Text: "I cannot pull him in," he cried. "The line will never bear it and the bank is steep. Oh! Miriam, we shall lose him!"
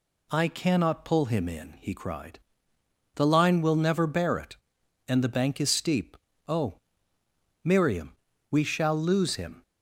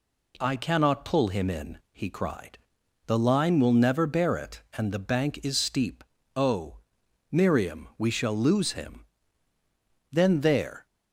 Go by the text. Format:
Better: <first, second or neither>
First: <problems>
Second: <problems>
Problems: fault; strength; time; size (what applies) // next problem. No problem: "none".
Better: first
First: none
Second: goes on to say "Then there"; noticeable; from 10.1 s on; 0.74 s long